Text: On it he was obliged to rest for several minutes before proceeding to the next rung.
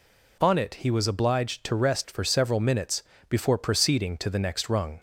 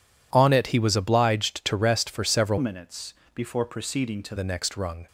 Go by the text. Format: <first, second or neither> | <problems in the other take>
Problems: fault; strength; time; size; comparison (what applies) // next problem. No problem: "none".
first | changes voice from "minutes" to "to"; from 2.5 to 4.3 s; 1.8 s long // pauses between "minutes" and "before"; slight; at 3.1 s; 0.20 s long; slight in the first